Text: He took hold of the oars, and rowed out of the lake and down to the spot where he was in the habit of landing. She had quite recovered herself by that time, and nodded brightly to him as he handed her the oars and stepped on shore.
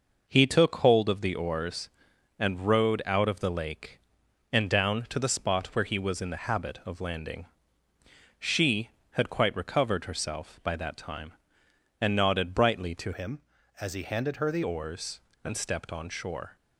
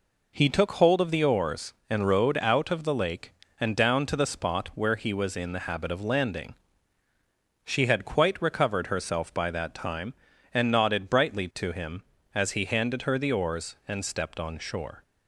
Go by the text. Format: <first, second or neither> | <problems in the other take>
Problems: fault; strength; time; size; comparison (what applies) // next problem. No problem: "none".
second | changes voice from "him" to "the"; from 13.1 to 14.6 s; 1.5 s long